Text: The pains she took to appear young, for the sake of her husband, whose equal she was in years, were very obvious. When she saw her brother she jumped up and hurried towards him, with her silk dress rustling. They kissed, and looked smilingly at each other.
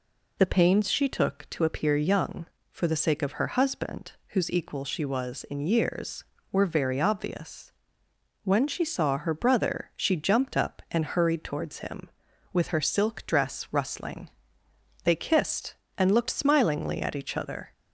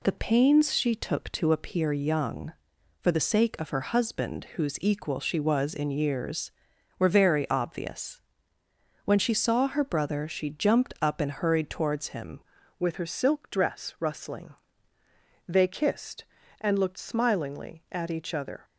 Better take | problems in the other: first | changes voice at "with"; from 12.7 s on; 5.9 s long

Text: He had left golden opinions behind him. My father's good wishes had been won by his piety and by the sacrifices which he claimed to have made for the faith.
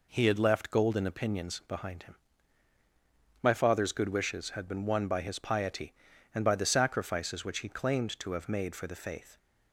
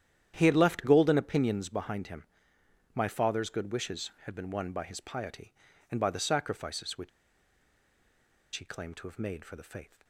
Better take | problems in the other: first | starts louder than the rest; strong; until 1.3 s; 10.5 dB // pauses between "which" and "he"; strong; at 7.0 s; 1.4 s long

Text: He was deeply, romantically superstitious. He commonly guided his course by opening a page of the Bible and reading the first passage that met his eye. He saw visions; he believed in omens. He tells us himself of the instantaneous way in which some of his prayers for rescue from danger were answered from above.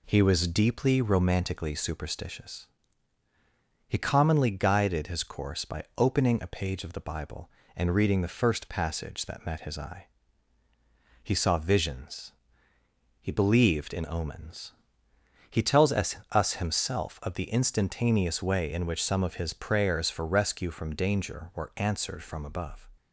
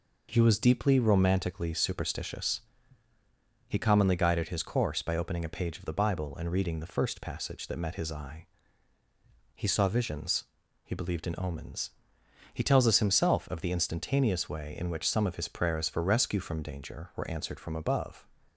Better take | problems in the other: second | says "us" twice; at 16.3 s

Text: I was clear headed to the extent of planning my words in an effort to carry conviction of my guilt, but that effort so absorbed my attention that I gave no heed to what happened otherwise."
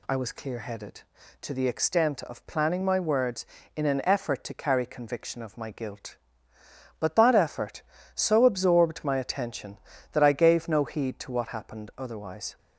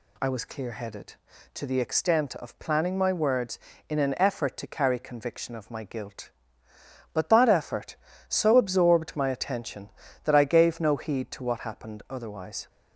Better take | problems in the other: neither | none

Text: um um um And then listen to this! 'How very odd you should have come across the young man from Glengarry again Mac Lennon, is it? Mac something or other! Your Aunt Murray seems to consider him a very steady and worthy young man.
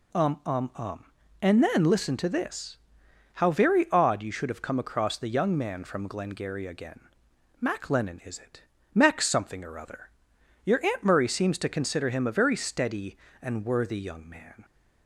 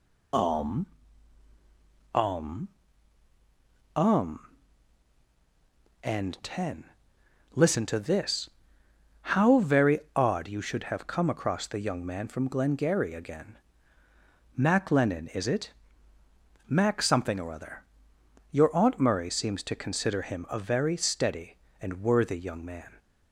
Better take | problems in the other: first | pauses between "um" and "um"; strong; at 0.8 s; 1.2 s long // pauses between "um" and "um"; strong; at 2.6 s; 1.2 s long // says "ten" for "then"; at 6.4 s // pauses between "very" and "odd"; slight; at 10.0 s; 0.16 s long // pauses between "again" and "Mac"; noticeable; at 13.5 s; 0.98 s long; noticeable in the first

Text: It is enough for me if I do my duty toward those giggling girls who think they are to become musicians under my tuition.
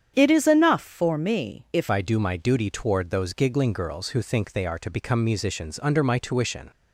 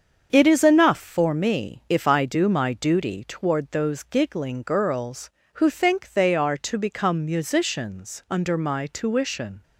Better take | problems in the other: second | starts louder than the rest; strong; until 1.1 s; 8.5 dB; also in the second // changes voice at "I"; from 1.9 s on; 4.8 s long

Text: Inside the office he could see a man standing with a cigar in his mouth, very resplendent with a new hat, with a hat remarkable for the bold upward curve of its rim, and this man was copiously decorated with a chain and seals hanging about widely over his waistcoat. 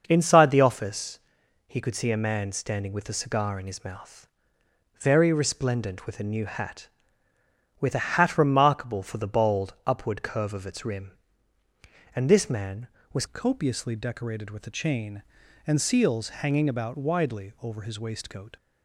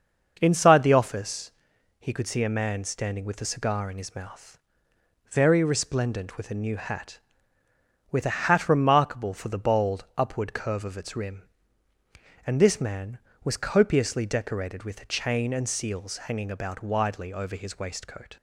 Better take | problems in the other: second | starts louder than the rest; until 1.0 s; 6 dB; also in the second // pauses between "office" and "he"; noticeable; at 1.1 s; 0.48 s long; noticeable in the second // changes voice at "copiously"; from 13.2 s on; 5.3 s long

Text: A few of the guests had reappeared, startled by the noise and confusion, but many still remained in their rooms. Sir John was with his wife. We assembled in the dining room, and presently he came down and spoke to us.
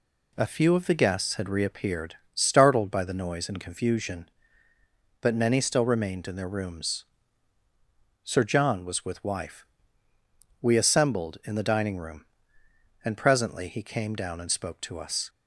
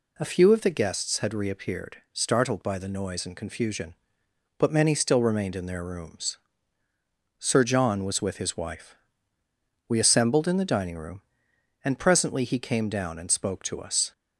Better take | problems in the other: second | skips "his"; at 9.2 s

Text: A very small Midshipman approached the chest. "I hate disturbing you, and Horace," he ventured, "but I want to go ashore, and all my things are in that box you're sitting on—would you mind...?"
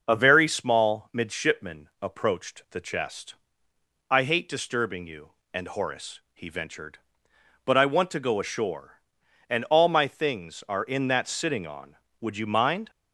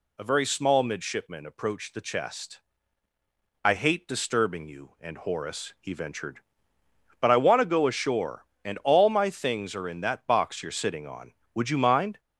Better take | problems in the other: second | starts louder than the rest; noticeable; until 1.0 s; 6 dB // skips "box you're"; at 11.2 s

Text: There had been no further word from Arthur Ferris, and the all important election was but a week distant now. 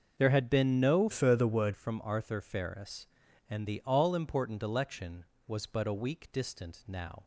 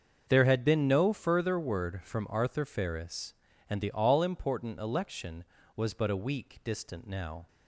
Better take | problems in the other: second | starts louder than the rest; noticeable; until 1.2 s; 6 dB; also in the second // changes voice from "further" to "word"; from 1.1 to 1.7 s; 0.6 s long

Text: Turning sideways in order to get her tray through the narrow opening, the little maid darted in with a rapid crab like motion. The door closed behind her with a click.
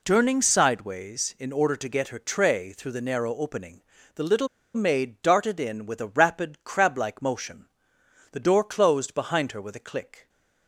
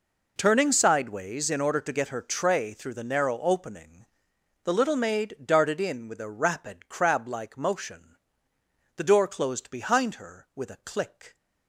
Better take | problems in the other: second | pauses between "little" and "maid"; slight; at 4.4 s; 0.27 s long

